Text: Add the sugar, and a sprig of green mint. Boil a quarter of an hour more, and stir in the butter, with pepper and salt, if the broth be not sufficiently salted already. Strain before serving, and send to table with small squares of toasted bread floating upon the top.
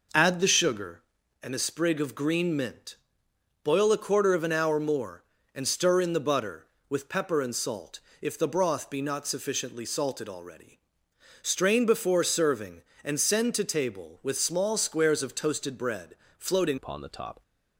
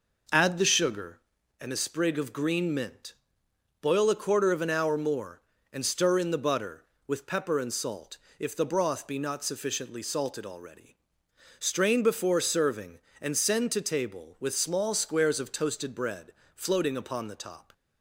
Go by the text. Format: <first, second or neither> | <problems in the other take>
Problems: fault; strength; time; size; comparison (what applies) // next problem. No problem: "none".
second | pauses between "bread" and "floating"; slight; at 16.1 s; 0.24 s long; slight in the second // changes voice at "upon"; from 16.7 s on; 0.7 s long